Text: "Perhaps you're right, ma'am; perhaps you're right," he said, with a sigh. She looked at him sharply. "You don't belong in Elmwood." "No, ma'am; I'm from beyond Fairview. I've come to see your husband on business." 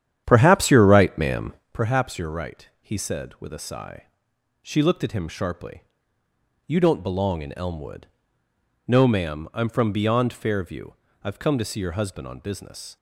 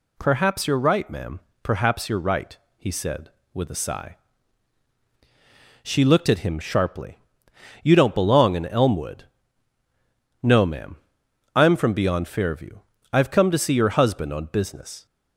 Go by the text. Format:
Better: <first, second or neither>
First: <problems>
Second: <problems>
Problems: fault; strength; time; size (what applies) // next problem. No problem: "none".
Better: second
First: starts louder than the rest; strong; until 1.7 s; 10 dB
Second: none